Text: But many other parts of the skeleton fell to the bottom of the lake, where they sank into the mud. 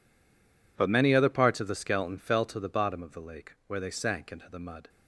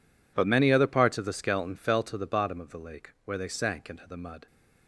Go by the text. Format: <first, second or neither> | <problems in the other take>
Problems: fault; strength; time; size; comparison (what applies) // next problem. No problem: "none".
second | stays silent before the first word; slight; until 0.7 s; 0.7 s long